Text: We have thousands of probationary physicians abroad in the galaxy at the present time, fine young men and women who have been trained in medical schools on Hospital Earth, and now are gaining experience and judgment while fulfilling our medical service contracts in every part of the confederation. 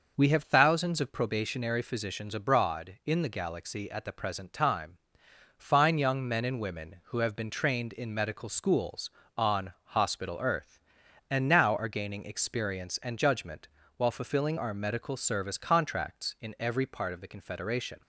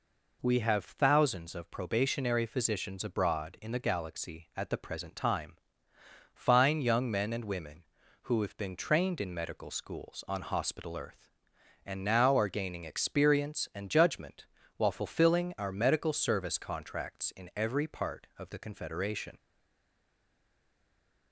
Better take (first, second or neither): first